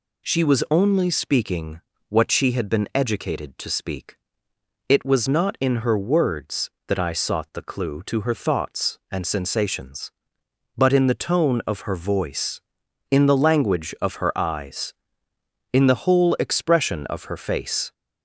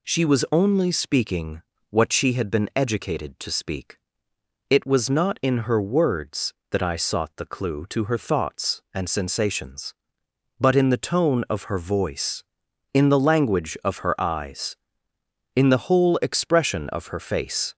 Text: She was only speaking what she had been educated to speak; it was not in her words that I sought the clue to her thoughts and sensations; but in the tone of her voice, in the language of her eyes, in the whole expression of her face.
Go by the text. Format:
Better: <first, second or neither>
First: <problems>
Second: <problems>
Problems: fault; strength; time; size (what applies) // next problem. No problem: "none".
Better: neither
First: pauses between "speaking" and "what"; slight; at 1.8 s; 0.28 s long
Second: pauses between "speaking" and "what"; slight; at 1.6 s; 0.28 s long